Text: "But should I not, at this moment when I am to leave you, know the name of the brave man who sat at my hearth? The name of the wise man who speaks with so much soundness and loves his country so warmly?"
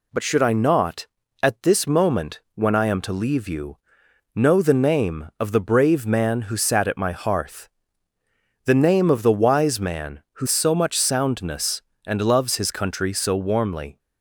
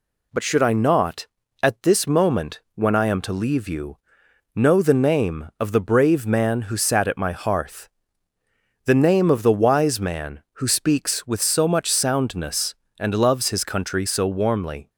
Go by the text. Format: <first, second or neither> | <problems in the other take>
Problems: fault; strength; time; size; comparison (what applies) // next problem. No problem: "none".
second | skips "speaks with"; at 10.4 s